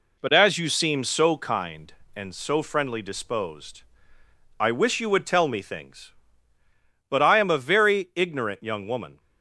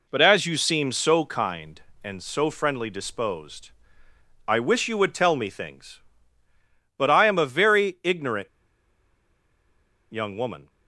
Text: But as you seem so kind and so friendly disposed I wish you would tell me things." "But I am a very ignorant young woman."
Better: first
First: pauses between "disposed" and "I"; noticeable; at 3.8 s; 0.78 s long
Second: pauses between "disposed" and "I"; noticeable; at 3.7 s; 0.78 s long // pauses between "ignorant" and "young"; strong; at 8.4 s; 1.6 s long

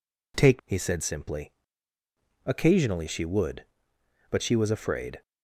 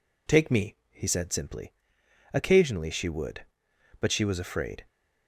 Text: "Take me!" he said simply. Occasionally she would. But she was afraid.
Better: second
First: skips "me"; at 0.6 s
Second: none

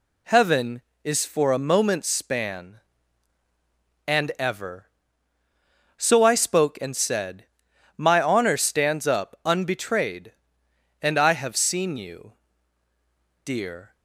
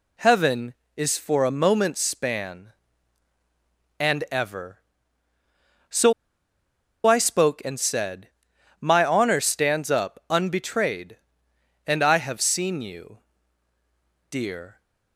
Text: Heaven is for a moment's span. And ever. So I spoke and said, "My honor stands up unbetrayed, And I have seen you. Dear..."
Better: first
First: none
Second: pauses between "So" and "I"; noticeable; at 6.1 s; 0.94 s long

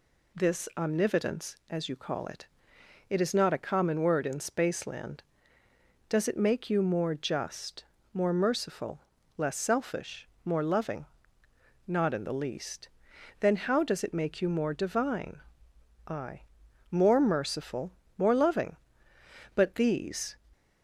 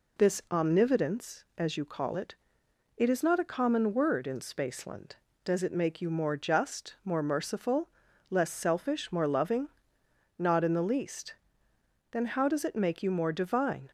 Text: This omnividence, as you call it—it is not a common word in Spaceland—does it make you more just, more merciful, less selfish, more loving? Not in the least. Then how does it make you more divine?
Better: second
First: goes on to say "I More merciful more loving But these"; strong; from 16.0 s on; 4.2 s long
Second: none

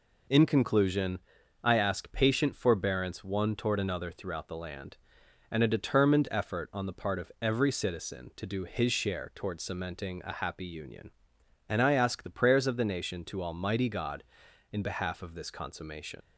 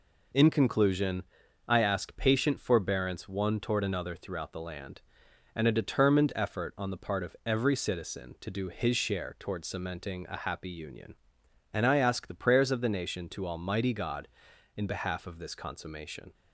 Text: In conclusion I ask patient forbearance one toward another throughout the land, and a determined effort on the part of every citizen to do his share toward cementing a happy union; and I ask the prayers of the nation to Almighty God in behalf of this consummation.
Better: second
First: pauses between "conclusion" and "I"; noticeable; at 1.1 s; 0.46 s long // leaves "consummation" unfinished; at 16.2 s; 90 ms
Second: pauses between "conclusion" and "I"; noticeable; at 1.2 s; 0.46 s long

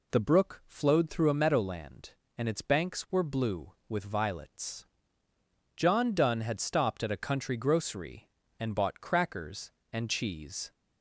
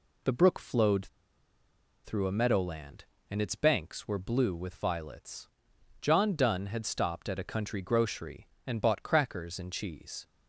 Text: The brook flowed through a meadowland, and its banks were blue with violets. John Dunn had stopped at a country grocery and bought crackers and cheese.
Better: first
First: none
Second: pauses between "flowed" and "through"; noticeable; at 1.0 s; 0.97 s long

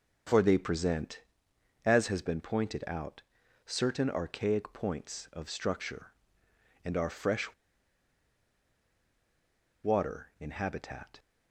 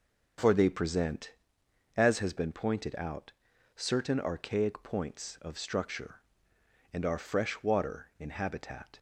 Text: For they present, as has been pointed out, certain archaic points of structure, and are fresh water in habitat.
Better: second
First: pauses between "fresh" and "water"; strong; at 7.5 s; 2.2 s long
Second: none

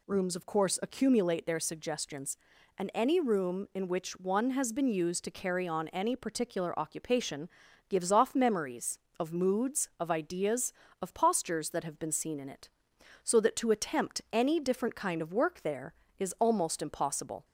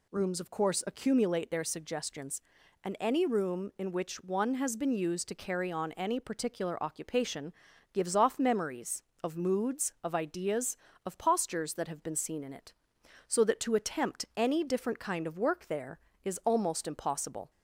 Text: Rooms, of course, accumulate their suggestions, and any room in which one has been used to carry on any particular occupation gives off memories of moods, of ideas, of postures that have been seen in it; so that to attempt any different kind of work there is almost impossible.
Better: neither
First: pauses between "occupation" and "gives"; at 7.4 s; 0.40 s long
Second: pauses between "occupation" and "gives"; at 7.5 s; 0.40 s long

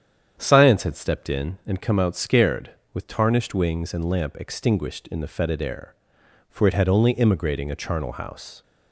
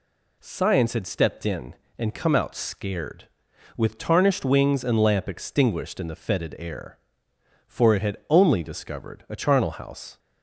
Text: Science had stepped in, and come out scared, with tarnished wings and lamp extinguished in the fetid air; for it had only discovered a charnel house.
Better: second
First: starts louder than the rest; strong; until 1.4 s; 9 dB // says "immigrating" for "discovered"; at 7.1 s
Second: none

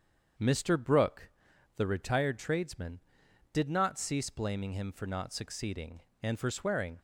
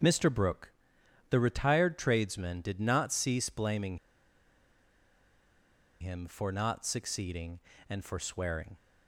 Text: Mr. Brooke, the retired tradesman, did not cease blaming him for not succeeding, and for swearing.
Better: first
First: starts louder than the rest; strong; until 1.8 s; 7.5 dB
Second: starts louder than the rest; noticeable; until 1.6 s; 6 dB // pauses between "blaming" and "him"; strong; at 3.9 s; 2.0 s long

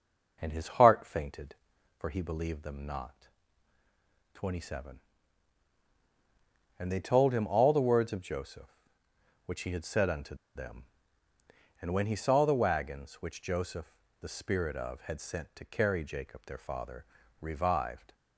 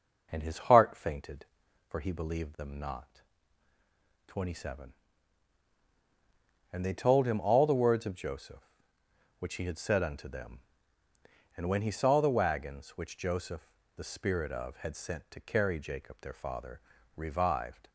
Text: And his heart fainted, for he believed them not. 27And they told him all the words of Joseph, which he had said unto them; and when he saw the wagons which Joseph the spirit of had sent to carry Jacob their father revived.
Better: second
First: pauses between "unto" and "them"; slight; at 10.3 s; 0.21 s long // pauses between "Joseph" and "the"; slight; at 13.9 s; 0.30 s long // pauses between "father" and "revived"; at 17.0 s; 0.38 s long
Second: pauses between "Joseph" and "the"; slight; at 13.6 s; 0.30 s long // pauses between "father" and "revived"; at 16.7 s; 0.38 s long

